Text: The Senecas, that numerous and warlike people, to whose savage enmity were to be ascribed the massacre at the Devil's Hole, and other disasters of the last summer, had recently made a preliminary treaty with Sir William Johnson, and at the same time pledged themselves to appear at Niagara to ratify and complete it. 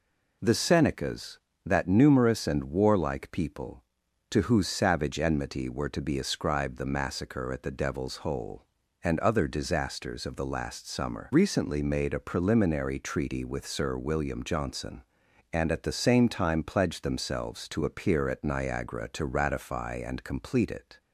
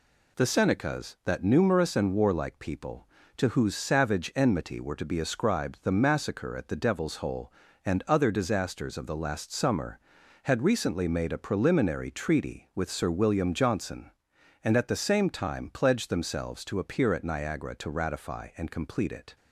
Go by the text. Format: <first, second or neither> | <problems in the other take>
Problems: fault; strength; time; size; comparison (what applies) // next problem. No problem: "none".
second | skips "had"; at 11.3 s